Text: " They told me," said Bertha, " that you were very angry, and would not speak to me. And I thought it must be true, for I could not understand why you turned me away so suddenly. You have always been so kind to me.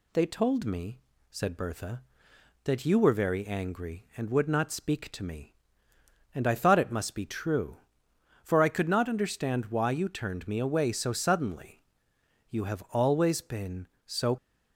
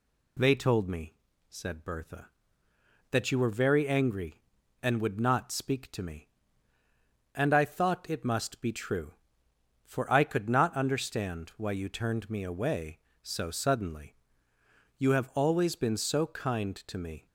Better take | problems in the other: second | stops before "kind to me"; at 14.3 s

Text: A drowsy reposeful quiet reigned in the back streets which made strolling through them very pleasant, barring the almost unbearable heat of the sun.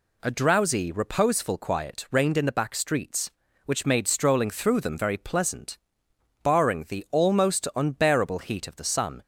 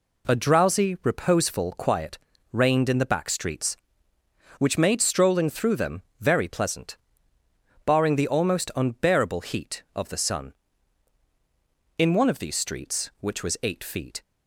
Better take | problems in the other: first | pauses between "quiet" and "reigned"; slight; at 2.1 s; 0.34 s long // pauses between "them" and "very"; slight; at 6.0 s; 0.18 s long // goes on to say "In one of these streets which was eight feet"; strong; from 11.9 s on; 2.2 s long

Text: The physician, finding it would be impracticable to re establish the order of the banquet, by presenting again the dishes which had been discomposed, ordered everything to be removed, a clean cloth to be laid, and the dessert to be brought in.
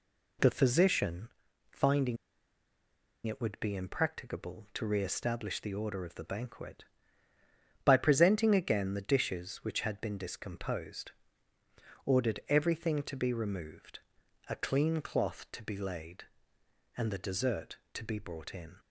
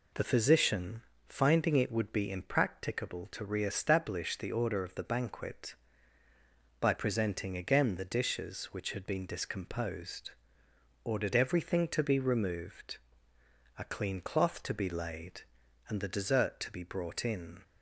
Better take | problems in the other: second | pauses between "finding" and "it"; at 2.1 s; 1.0 s long

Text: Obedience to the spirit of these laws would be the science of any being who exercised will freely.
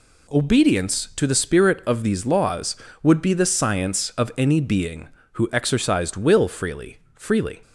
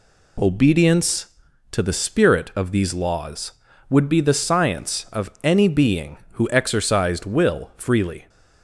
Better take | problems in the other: second | says "freely" twice; at 7.1 s

